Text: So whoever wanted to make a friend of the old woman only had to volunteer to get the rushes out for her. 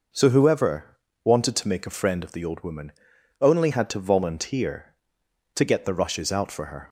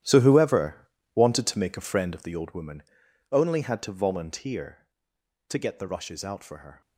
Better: first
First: pauses between "whoever" and "wanted"; slight; at 0.9 s; 0.26 s long // pauses between "woman" and "only"; noticeable; at 2.9 s; 0.48 s long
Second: gets quieter; strong; throughout; 12 dB // pauses between "whoever" and "wanted"; slight; at 0.8 s; 0.26 s long // pauses between "woman" and "only"; noticeable; at 2.8 s; 0.48 s long

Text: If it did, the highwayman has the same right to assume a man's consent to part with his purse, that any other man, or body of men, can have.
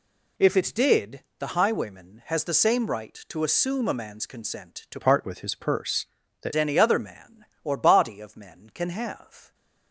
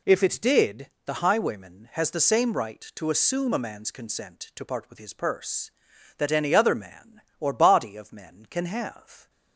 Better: second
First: changes voice from "part" to "that"; from 5.0 to 6.5 s; 1.5 s long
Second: none

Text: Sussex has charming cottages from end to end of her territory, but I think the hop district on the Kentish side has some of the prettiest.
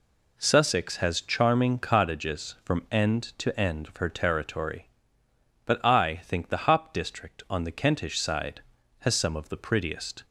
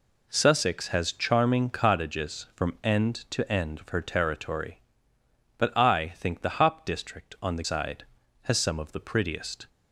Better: first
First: none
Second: skips "Kentish"; at 7.6 s

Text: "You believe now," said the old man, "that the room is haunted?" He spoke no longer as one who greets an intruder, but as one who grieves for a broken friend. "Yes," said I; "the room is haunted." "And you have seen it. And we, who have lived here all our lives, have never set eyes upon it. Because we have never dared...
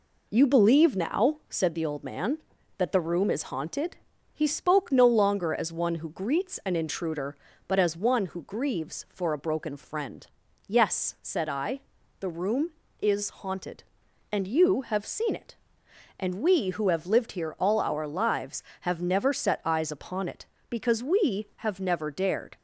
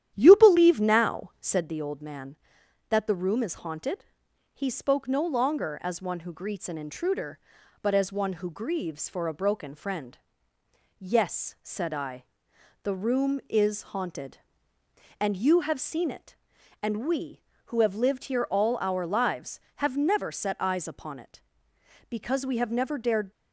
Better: first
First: none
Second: starts louder than the rest; strong; until 1.6 s; 11 dB

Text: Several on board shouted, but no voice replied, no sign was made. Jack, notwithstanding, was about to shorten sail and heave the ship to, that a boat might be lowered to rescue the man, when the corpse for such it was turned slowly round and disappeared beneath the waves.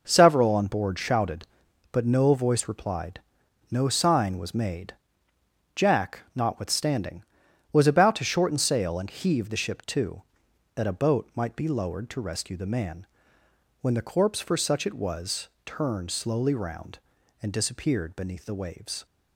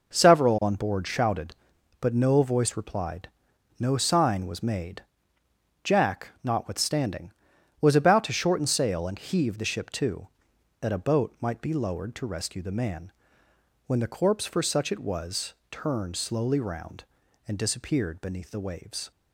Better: neither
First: pauses between "was" and "turned"; slight; at 15.4 s; 0.20 s long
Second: pauses between "was" and "turned"; slight; at 15.5 s; 0.20 s long

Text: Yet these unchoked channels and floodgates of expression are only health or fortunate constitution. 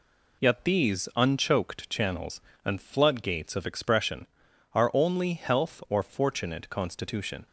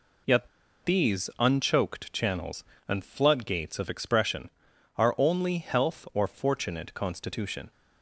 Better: first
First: none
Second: pauses between "Yet" and "these"; at 0.4 s; 0.36 s long

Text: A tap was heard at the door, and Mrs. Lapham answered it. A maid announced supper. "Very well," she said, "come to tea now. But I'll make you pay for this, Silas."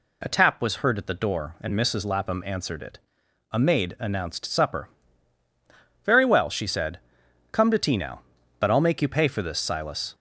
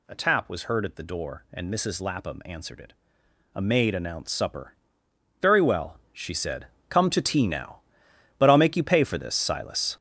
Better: first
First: none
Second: gets louder; strong; throughout; 9 dB

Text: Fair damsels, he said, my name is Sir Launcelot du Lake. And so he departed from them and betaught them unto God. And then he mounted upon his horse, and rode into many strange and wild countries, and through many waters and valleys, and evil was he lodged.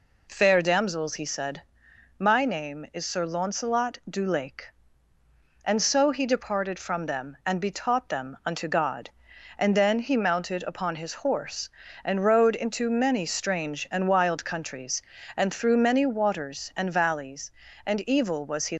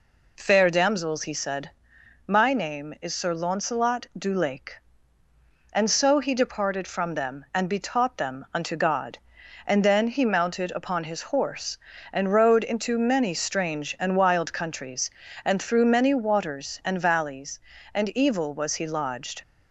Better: second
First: stops before "lodged"; at 18.7 s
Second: none

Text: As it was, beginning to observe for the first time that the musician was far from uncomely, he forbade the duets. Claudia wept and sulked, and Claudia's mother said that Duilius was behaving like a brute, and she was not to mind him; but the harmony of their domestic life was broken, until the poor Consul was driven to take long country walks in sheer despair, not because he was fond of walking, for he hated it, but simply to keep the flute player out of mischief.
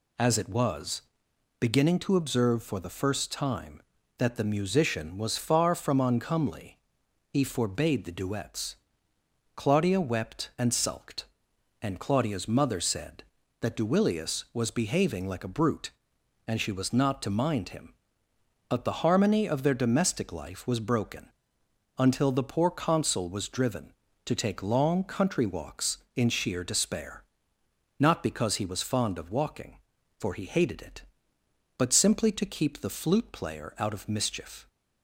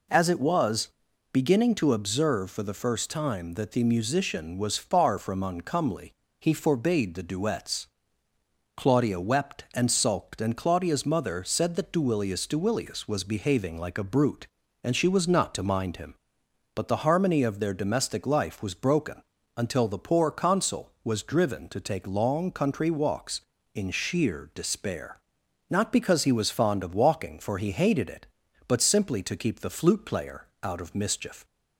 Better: first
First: none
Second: says "Duilius" twice; at 12.4 s // pauses between "player" and "out"; slight; at 30.4 s; 0.16 s long

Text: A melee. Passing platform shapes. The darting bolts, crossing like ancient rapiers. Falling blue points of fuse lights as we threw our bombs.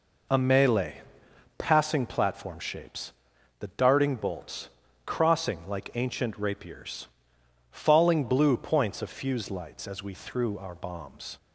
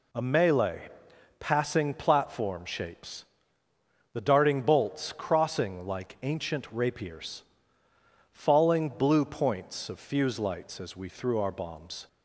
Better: neither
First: none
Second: none

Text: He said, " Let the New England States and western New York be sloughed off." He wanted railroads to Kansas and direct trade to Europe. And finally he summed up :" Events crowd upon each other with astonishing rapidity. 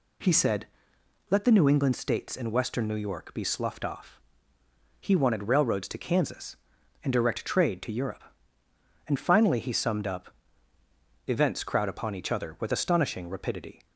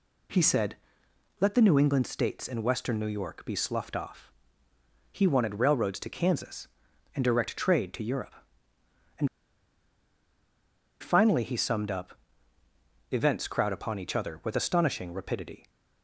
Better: first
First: none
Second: pauses between "And" and "finally"; strong; at 9.2 s; 1.7 s long

